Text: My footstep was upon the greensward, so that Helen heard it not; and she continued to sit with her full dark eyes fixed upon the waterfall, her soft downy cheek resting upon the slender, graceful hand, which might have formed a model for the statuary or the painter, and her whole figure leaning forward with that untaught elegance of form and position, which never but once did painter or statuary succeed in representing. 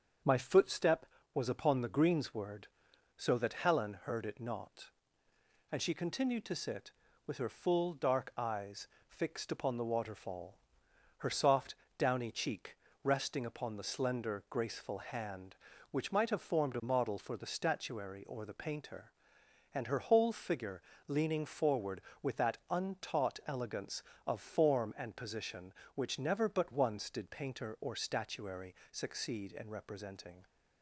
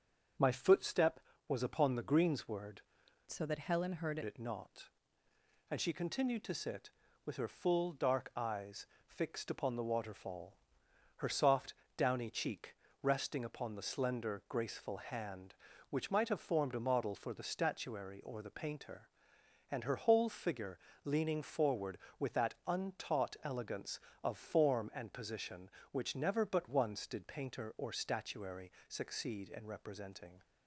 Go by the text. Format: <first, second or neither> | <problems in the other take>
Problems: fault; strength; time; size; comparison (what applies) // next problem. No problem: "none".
first | starts louder than the rest; strong; until 1.6 s; 7 dB; strong in the first // changes voice from "so" to "heard"; from 3.3 to 4.1 s; 0.8 s long // pauses between "eyes" and "fixed"; slight; at 8.8 s; 0.18 s long; slight in the first // pauses between "soft" and "downy"; slight; at 11.7 s; 0.22 s long; slight in the first // pauses between "cheek" and "resting"; slight; at 12.7 s; 0.26 s long; slight in the first // pauses between "figure" and "leaning"; slight; at 20.7 s; 0.28 s long; slight in the first // pauses between "statuary" and "succeed"; slight; at 28.6 s; 0.20 s long; slight in the first